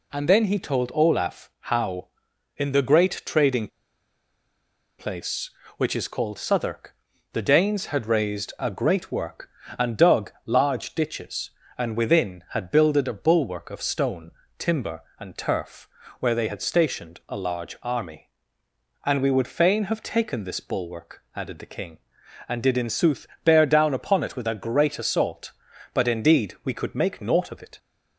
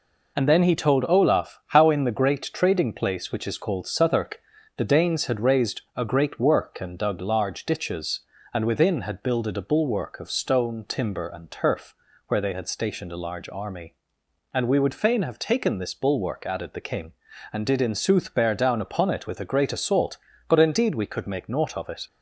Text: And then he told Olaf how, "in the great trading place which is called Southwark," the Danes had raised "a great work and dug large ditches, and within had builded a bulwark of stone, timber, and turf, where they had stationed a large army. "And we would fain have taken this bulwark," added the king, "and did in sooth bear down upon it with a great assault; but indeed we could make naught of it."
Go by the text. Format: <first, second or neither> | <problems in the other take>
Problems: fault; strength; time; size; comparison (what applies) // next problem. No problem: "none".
second | pauses between "trading" and "place"; strong; at 3.6 s; 1.3 s long // pauses between "sooth" and "bear"; slight; at 23.2 s; 0.16 s long